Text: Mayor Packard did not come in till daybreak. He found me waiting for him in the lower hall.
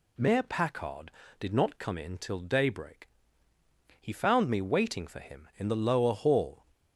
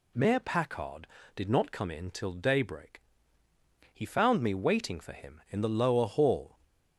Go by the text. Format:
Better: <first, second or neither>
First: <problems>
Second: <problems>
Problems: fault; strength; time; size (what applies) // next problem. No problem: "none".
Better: neither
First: none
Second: none